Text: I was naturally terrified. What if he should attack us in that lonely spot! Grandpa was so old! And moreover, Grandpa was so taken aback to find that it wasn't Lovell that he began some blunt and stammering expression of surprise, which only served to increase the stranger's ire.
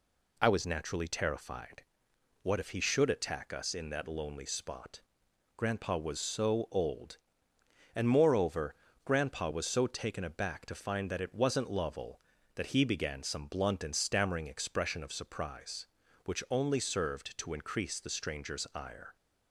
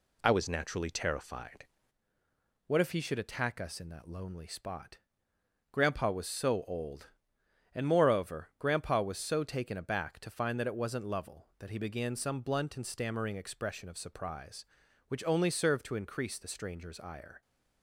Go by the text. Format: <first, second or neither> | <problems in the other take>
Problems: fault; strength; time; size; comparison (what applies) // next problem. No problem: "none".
first | changes voice at "What"; from 2.6 s on; 14.8 s long